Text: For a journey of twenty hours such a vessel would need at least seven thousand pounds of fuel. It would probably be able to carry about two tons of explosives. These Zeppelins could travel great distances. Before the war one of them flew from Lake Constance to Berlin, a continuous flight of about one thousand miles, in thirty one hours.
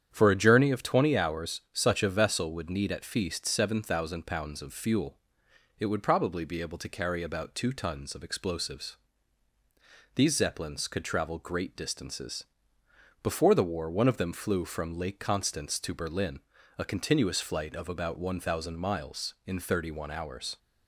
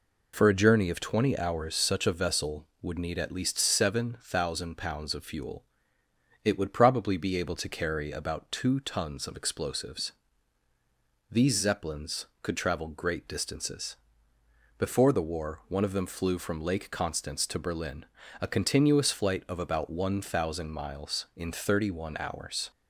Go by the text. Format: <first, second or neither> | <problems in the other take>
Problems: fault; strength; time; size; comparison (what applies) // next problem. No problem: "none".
second | starts louder than the rest; strong; until 1.1 s; 9 dB // says "feast" for "least"; at 3.0 s